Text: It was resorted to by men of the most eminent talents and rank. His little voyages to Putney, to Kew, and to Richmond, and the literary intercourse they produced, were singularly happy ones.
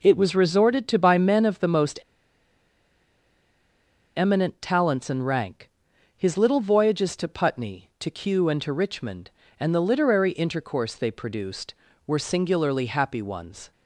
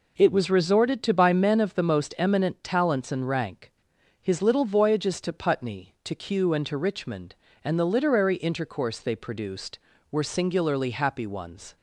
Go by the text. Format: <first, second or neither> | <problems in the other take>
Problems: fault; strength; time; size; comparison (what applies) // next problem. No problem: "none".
second | pauses between "most" and "eminent"; strong; at 1.9 s; 2.1 s long